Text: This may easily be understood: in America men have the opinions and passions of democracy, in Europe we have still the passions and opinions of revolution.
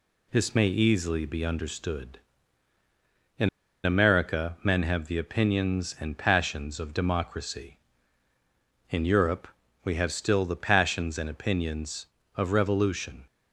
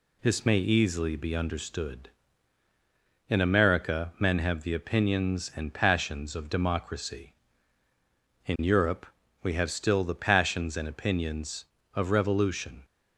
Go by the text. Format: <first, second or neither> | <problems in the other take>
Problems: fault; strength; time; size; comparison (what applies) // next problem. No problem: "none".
second | pauses between "in" and "America"; slight; at 3.4 s; 0.35 s long // pauses between "Europe" and "we"; slight; at 9.4 s; 0.34 s long; slight in the second